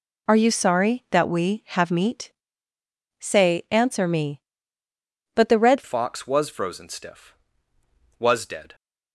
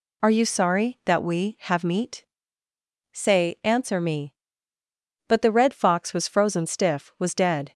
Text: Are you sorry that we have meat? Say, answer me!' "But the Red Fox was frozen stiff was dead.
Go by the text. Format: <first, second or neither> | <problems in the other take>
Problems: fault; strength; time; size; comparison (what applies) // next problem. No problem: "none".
second | changes voice at "Fox"; from 5.8 s on; 2.9 s long